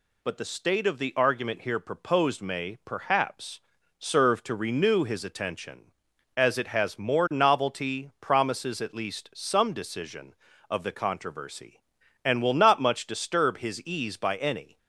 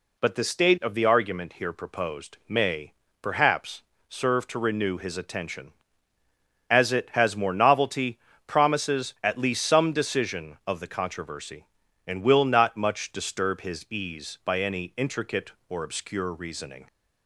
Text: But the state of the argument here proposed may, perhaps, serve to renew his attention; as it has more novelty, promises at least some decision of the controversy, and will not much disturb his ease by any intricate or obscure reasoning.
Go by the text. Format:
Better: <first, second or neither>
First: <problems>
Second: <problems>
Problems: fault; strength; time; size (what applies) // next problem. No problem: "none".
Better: second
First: stops before "intricate or obscure reasoning"; at 14.7 s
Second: none